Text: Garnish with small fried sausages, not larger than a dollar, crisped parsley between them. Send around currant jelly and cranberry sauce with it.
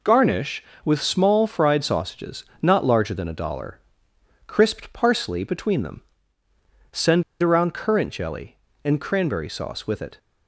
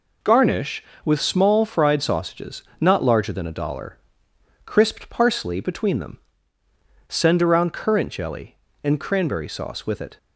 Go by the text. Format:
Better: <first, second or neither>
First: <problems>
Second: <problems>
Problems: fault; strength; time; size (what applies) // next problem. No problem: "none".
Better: second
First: pauses between "Send" and "around"; slight; at 7.2 s; 0.18 s long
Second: none